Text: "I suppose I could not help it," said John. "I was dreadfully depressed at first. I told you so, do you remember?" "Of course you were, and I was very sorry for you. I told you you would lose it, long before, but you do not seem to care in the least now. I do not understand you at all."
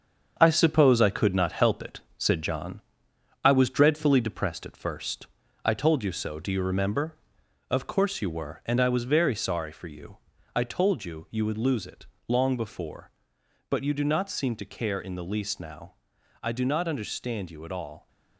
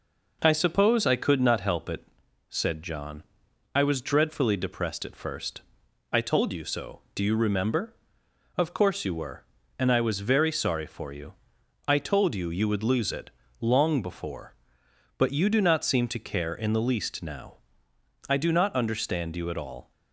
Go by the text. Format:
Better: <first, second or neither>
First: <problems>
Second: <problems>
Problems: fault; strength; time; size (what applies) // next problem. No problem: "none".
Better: second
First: gets quieter; throughout; 7 dB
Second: none